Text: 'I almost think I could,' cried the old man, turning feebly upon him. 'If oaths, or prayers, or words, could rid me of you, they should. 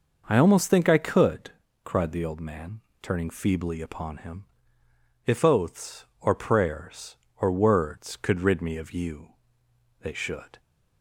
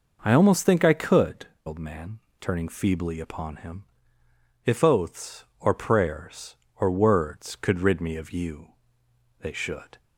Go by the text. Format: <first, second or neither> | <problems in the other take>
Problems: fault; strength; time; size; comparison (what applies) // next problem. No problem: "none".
first | skips "cried the"; at 1.5 s